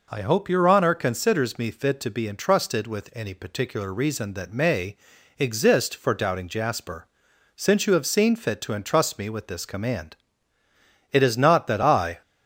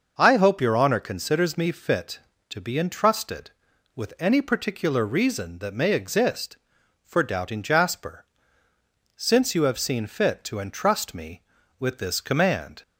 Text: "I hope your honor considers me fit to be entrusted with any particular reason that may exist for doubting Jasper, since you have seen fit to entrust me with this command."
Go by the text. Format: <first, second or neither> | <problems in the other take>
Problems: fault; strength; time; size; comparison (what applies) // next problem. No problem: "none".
second | pauses between "may" and "exist"; at 4.9 s; 0.40 s long // goes on to say "It is not that I"; noticeable; from 11.1 s on; 1.1 s long